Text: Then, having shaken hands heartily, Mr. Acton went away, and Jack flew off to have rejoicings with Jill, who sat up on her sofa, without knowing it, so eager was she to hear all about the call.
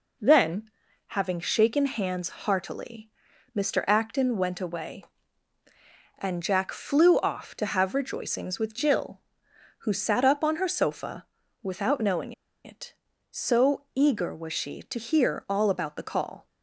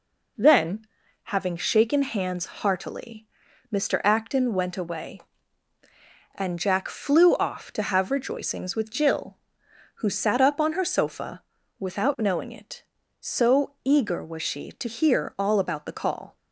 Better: second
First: pauses between "knowing" and "it"; slight; at 12.3 s; 0.32 s long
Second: none

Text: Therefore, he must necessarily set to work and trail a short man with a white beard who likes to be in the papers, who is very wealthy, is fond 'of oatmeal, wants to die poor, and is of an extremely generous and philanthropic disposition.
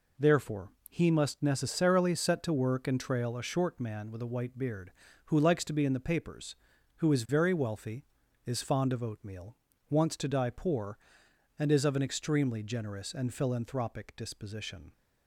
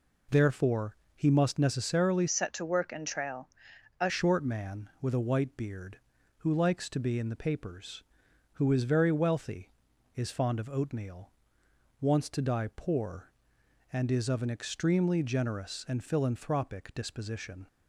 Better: first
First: none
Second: changes voice from "set" to "a"; from 2.2 to 4.0 s; 1.8 s long // pauses between "trail" and "a"; noticeable; at 3.4 s; 0.50 s long

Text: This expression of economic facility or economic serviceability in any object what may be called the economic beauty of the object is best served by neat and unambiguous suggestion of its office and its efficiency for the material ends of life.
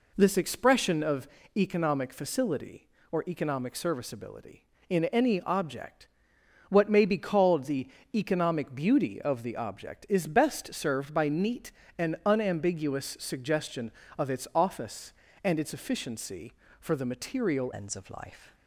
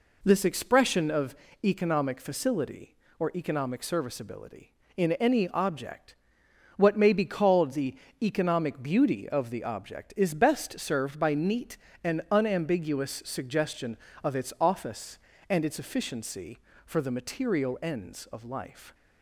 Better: second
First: pauses between "of" and "economic"; slight; at 1.2 s; 0.30 s long // pauses between "object" and "what"; noticeable; at 6.0 s; 0.64 s long // pauses between "the" and "economic"; slight; at 7.8 s; 0.28 s long // changes voice at "ends"; from 17.7 s on; 0.8 s long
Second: pauses between "of" and "economic"; slight; at 1.3 s; 0.30 s long // pauses between "object" and "what"; noticeable; at 6.1 s; 0.64 s long // pauses between "the" and "economic"; slight; at 7.9 s; 0.28 s long

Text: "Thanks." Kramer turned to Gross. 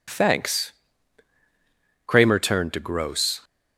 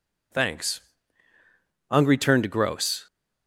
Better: first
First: none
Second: says "Ungry" for "Kramer"; at 1.8 s

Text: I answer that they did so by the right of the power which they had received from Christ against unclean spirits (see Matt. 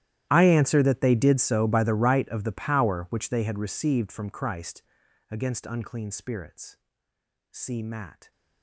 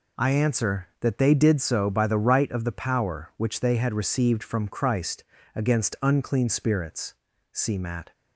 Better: second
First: gets quieter; strong; throughout; 23.5 dB // pauses between "Christ" and "against"; noticeable; at 4.8 s; 0.48 s long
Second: pauses between "Christ" and "against"; slight; at 5.2 s; 0.30 s long

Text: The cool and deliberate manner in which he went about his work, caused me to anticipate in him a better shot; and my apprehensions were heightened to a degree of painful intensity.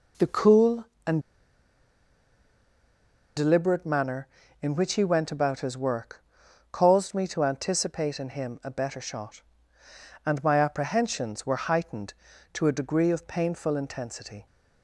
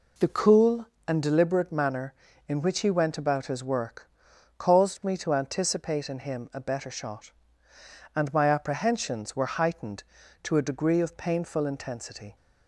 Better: second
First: pauses between "and" and "deliberate"; strong; at 1.2 s; 2.1 s long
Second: none

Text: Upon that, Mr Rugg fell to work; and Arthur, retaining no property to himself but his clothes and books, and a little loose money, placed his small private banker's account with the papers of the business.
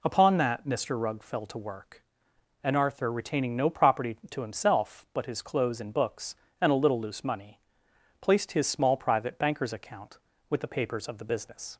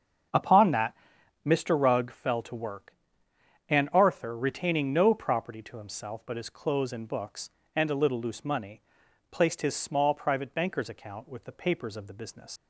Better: first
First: none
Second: starts louder than the rest; until 1.7 s; 7 dB // leaves "business" unfinished; at 12.5 s; 125 ms

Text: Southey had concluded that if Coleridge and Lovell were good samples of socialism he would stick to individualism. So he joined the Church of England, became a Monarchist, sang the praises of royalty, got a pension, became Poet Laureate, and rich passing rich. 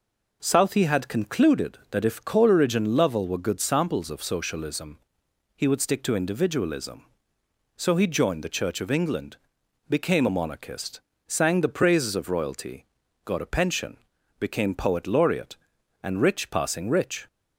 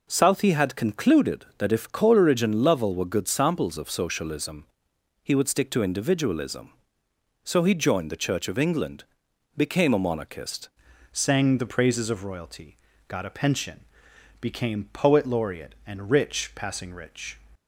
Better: first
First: pauses between "socialism" and "he"; noticeable; at 4.9 s; 0.56 s long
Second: pauses between "socialism" and "he"; noticeable; at 4.6 s; 0.56 s long // changes voice at "sang"; from 11.1 s on; 6.2 s long

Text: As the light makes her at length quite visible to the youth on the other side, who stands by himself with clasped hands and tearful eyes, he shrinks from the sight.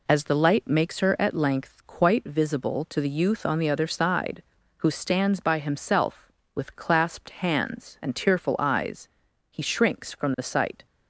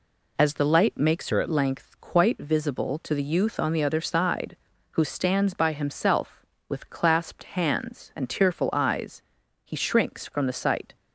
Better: first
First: none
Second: changes voice from "her" to "at"; from 1.3 to 1.4 s; 0.1 s long

